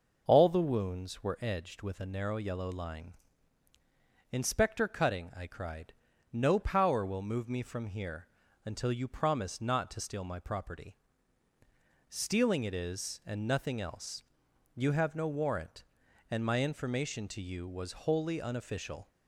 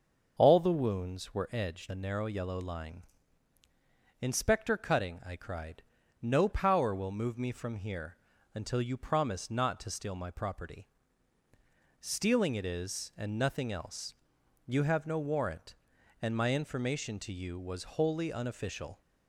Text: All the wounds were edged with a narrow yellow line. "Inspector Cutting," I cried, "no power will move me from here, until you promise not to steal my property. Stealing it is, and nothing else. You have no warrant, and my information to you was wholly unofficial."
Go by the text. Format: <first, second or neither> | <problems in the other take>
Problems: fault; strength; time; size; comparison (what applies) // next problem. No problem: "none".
first | starts louder than the rest; until 1.3 s; 6.5 dB // skips "with"; at 1.8 s